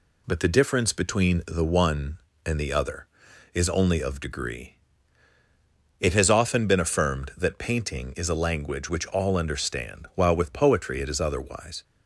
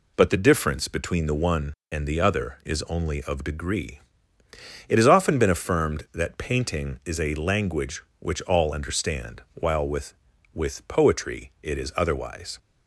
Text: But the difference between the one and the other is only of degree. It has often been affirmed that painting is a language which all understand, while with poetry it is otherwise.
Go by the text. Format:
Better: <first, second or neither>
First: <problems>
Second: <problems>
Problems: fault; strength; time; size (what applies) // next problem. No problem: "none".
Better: first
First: none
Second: says "with" twice; at 10.5 s